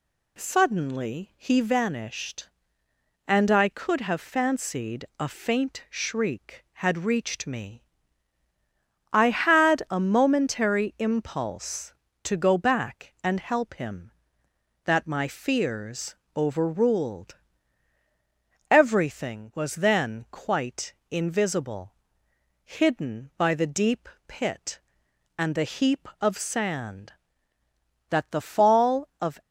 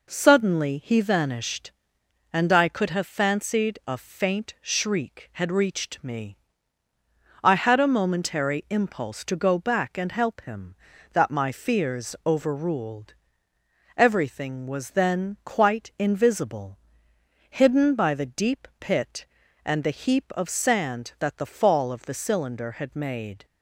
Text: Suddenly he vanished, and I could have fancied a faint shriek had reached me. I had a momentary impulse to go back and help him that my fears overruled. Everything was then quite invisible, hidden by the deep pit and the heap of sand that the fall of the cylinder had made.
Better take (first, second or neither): second